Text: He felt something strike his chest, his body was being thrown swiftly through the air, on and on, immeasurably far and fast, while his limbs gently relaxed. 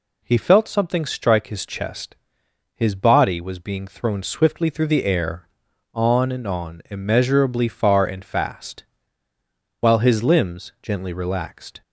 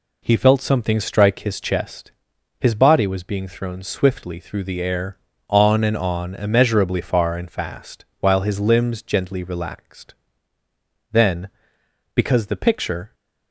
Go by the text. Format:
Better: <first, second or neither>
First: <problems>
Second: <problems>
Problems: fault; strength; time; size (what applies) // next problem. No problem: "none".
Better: first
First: none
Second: goes on to say "Then because the picture"; strong; from 11.1 s on; 2.0 s long